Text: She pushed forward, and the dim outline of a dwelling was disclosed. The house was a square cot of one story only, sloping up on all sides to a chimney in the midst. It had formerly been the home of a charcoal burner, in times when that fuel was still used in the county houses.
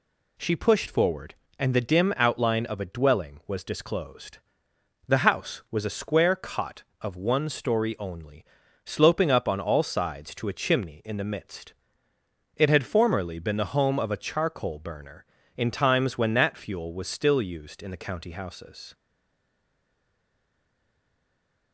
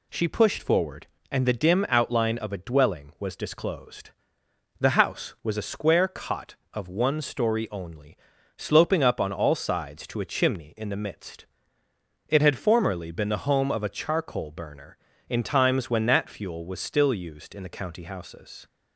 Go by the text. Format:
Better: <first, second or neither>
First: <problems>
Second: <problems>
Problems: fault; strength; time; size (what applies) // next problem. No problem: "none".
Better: second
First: stays silent after the last word; strong; from 18.9 s on; 2.8 s long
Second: none